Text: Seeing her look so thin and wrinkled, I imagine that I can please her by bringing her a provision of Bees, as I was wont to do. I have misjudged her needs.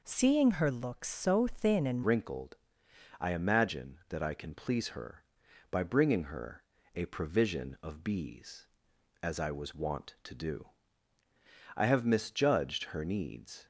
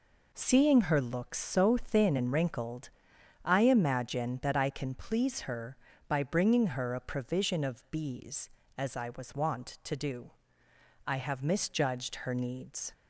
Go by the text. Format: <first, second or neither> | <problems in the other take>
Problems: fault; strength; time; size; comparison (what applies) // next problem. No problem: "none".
second | changes voice at "wrinkled"; from 2.0 s on; 11.6 s long // pauses between "her" and "a"; slight; at 6.6 s; 0.32 s long